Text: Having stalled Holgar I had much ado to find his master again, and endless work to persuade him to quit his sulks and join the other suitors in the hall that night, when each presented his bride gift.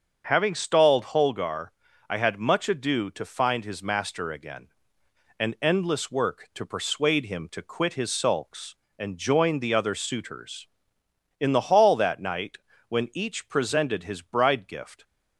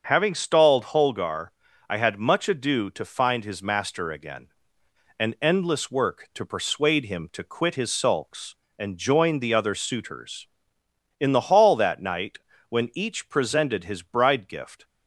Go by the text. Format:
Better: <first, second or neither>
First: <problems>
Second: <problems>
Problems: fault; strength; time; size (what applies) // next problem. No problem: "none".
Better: neither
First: starts louder than the rest; until 1.2 s; 6.5 dB // pauses between "Holgar" and "I"; at 1.6 s; 0.42 s long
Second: starts louder than the rest; until 1.0 s; 6.5 dB // pauses between "Holgar" and "I"; at 1.4 s; 0.42 s long